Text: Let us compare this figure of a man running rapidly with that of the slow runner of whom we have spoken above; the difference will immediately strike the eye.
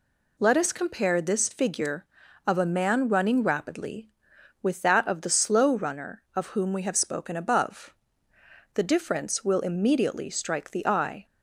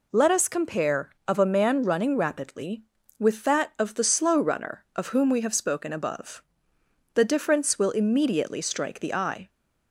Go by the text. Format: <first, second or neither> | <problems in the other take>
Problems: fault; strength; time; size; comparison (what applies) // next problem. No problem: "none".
first | skips "this figure"; at 1.1 s